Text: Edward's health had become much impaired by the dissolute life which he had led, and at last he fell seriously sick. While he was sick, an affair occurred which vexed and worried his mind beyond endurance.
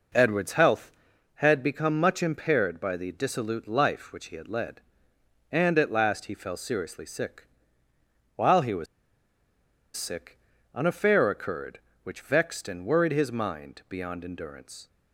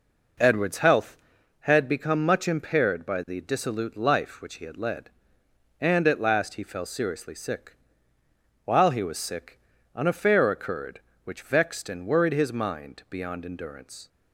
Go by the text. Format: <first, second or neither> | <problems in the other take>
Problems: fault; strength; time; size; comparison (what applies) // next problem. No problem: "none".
second | pauses between "was" and "sick"; at 8.8 s; 1.1 s long